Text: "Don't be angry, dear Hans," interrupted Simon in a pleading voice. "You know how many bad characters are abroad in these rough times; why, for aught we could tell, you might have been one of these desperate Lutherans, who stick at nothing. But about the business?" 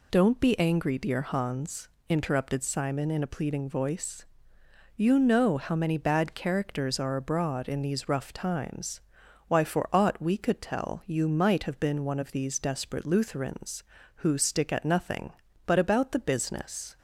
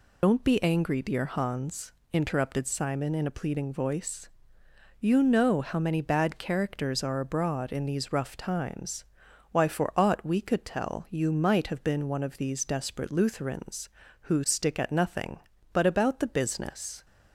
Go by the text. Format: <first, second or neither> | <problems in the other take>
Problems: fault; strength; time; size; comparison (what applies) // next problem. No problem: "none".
first | loses the start of "Don't"; at 0.2 s; 70 ms